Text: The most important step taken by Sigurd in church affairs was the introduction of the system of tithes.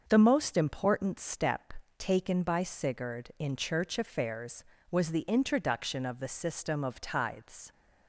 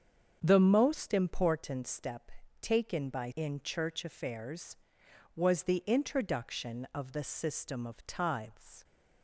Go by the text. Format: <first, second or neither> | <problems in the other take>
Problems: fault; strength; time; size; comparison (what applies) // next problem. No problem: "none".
first | starts louder than the rest; strong; until 1.4 s; 7 dB; also in the first // pauses between "step" and "taken"; slight; at 2.2 s; 0.32 s long; slight in the first // skips "Sigurd"; at 3.3 s